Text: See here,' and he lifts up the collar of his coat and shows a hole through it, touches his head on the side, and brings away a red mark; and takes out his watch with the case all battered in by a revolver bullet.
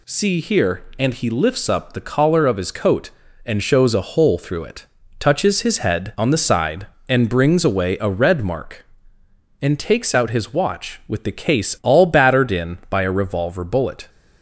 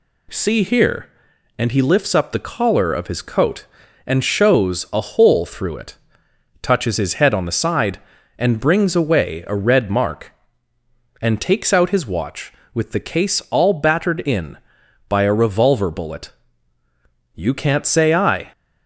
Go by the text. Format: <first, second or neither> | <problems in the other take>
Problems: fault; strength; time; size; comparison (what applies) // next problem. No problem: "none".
first | goes on to say "You can't say I"; noticeable; from 17.3 s on; 1.1 s long